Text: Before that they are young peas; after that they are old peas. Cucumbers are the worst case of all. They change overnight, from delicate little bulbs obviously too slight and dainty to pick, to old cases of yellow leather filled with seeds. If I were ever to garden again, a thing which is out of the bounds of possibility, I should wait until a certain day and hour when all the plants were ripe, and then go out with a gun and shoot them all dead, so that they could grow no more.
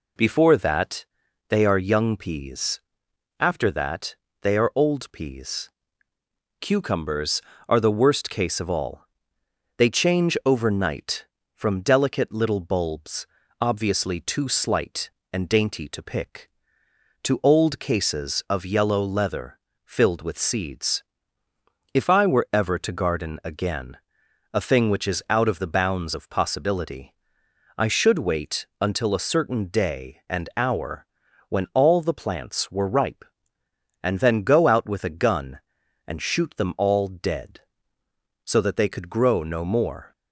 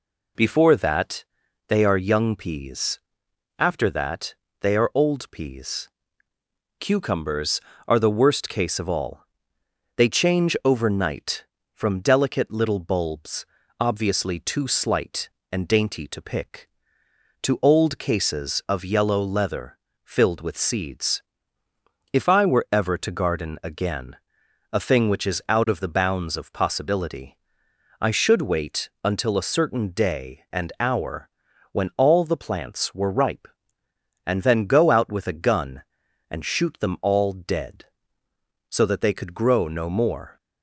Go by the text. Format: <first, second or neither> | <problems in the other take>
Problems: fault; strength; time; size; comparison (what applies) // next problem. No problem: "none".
neither | pauses between "that" and "they"; the same in both // pauses between "that" and "they"; slight; the same in both // pauses between "bulbs" and "obviously"; slight; the same in both // pauses between "leather" and "filled"; slight; the same in both // pauses between "hour" and "when"; the same in both